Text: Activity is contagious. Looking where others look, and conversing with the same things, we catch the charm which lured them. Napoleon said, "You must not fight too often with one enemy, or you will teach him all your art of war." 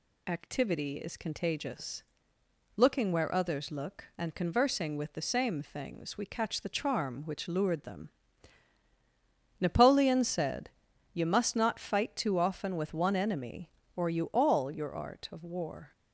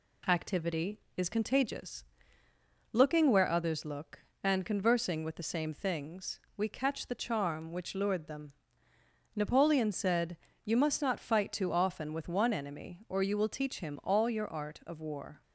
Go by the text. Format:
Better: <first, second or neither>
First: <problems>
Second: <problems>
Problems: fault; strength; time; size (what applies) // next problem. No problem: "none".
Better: second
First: skips "will teach him"; at 14.2 s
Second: none